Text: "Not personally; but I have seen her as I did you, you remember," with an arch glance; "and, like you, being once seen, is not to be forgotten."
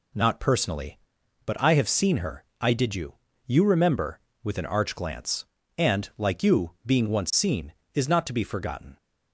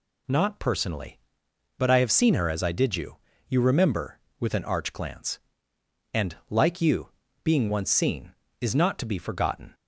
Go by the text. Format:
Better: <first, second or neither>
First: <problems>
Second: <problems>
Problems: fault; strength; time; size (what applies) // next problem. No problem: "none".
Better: second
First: skips "as"; at 2.5 s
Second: none